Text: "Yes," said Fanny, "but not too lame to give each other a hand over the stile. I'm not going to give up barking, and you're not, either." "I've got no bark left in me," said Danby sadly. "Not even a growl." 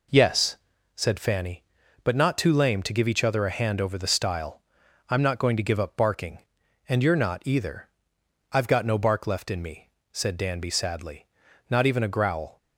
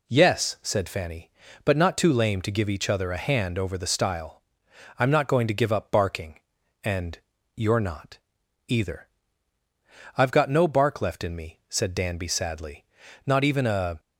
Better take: first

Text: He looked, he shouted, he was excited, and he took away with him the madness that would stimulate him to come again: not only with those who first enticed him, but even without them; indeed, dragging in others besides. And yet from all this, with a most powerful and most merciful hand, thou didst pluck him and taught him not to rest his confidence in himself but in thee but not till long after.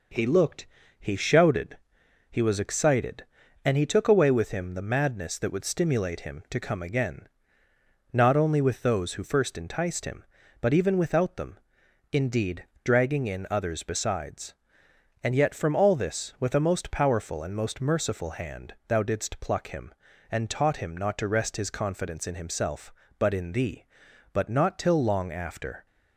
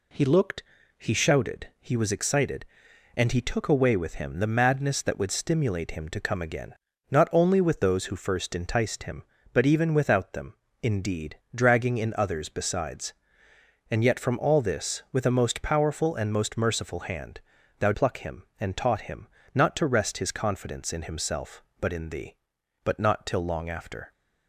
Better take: first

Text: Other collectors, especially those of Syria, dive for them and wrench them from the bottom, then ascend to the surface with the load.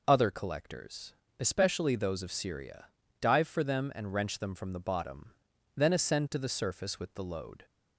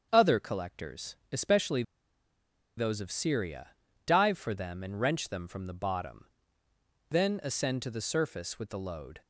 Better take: first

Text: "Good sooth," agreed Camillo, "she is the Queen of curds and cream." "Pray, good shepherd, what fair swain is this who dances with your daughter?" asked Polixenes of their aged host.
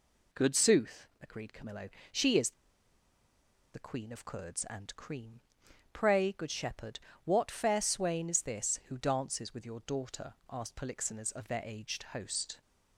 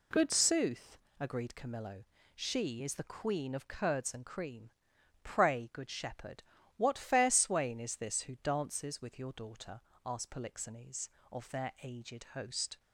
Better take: second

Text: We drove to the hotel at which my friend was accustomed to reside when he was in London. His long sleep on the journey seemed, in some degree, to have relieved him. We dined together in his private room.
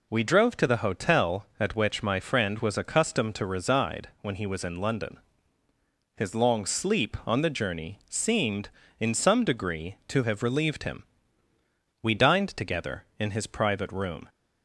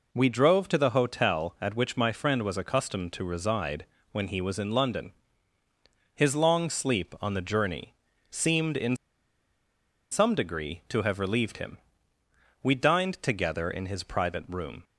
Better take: first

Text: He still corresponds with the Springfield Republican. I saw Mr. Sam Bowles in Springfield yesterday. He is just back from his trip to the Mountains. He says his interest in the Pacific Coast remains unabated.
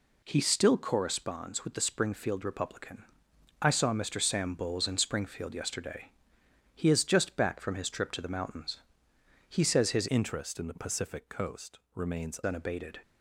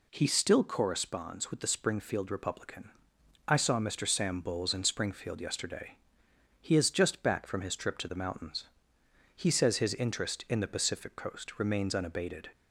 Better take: second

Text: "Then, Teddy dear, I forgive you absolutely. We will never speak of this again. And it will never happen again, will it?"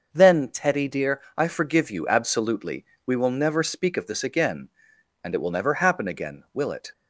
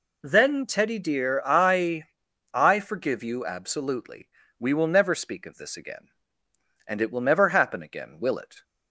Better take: first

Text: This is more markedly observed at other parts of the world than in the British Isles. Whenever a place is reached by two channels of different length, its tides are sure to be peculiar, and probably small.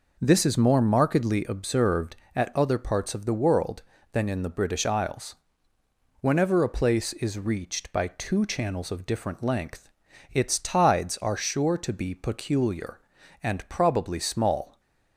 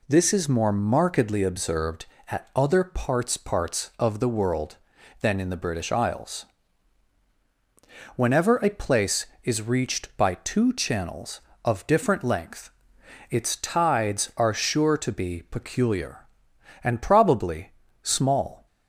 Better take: first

